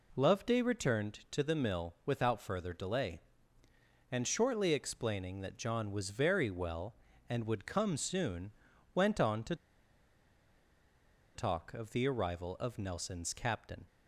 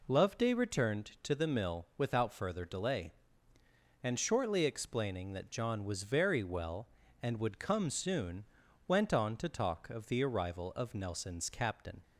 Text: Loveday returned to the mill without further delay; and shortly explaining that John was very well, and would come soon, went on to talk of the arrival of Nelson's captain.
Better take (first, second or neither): second